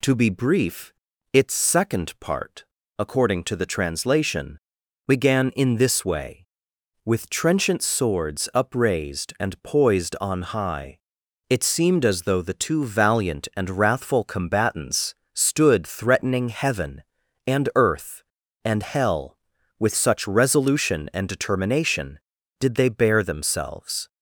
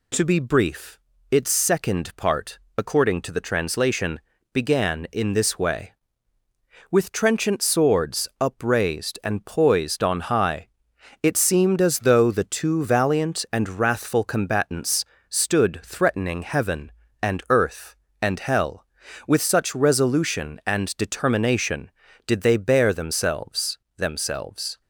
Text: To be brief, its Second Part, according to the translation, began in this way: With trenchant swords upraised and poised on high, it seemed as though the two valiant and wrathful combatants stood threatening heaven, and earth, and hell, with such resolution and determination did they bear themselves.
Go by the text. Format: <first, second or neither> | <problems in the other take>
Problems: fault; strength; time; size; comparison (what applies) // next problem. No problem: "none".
first | pauses between "combatants" and "stood"; slight; at 15.0 s; 0.24 s long; slight in the first // says "themselves" twice; at 23.9 s